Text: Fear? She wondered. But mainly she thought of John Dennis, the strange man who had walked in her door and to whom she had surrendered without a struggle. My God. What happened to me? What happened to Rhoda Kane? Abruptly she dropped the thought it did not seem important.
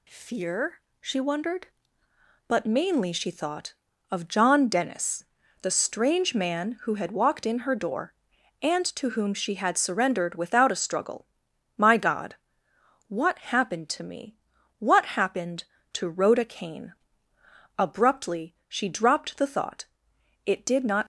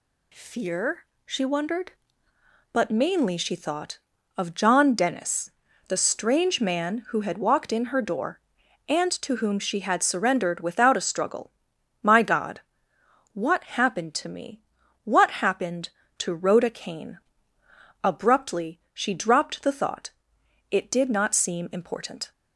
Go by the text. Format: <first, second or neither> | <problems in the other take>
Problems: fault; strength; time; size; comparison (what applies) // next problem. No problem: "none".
second | pauses between "thought" and "it"; noticeable; at 19.8 s; 0.60 s long; noticeable in the second // stops before "seem important"; at 21.0 s